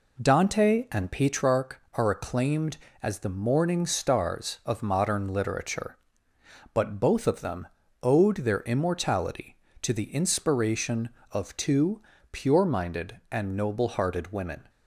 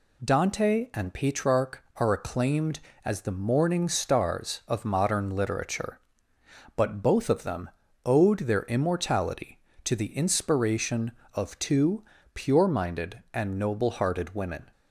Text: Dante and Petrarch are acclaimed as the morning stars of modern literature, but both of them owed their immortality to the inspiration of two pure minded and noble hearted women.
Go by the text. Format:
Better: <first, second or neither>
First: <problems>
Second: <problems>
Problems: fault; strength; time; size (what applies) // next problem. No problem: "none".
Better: second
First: starts louder than the rest; until 1.5 s; 3.5 dB // pauses between "them" and "owed"; slight; at 7.6 s; 0.34 s long // pauses between "two" and "pure"; slight; at 12.0 s; 0.30 s long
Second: pauses between "them" and "owed"; slight; at 7.6 s; 0.34 s long // pauses between "two" and "pure"; slight; at 12.0 s; 0.30 s long